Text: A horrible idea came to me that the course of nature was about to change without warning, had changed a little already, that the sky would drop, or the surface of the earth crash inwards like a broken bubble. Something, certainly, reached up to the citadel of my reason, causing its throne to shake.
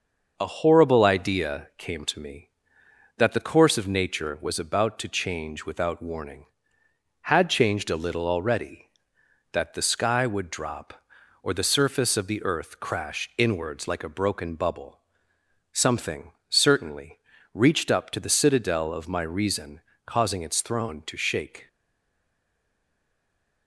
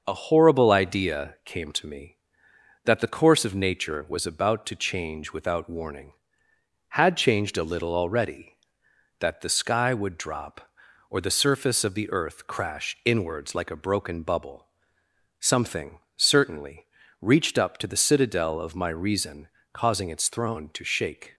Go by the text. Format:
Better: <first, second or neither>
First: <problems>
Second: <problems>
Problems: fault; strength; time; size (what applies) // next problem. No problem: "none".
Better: second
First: starts louder than the rest; until 1.3 s; 6 dB // stays silent after the last word; noticeable; from 21.6 s on; 2.0 s long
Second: starts louder than the rest; until 1.0 s; 6 dB